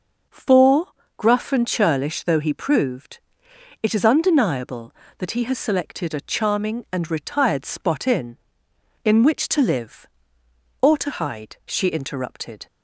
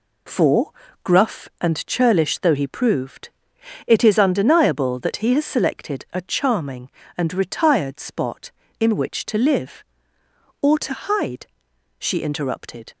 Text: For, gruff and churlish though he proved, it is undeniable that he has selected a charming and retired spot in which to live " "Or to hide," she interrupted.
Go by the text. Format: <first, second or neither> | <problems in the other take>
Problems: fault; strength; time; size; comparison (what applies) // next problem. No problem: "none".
second | starts louder than the rest; until 1.5 s; 6 dB // says "in" twice; at 9.0 s